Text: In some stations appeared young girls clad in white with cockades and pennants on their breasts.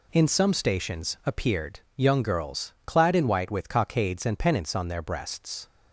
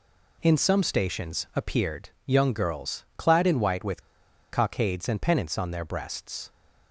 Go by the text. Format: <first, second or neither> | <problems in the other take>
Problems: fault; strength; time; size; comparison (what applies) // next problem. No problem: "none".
first | pauses between "with" and "cockades"; noticeable; at 4.0 s; 0.50 s long